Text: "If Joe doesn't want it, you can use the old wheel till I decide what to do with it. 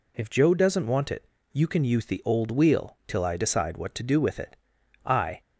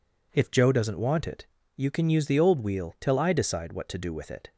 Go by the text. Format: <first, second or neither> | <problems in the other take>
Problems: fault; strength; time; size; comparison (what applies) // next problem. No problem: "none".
second | goes on to say "I"; slight; from 5.0 s on; 0.36 s long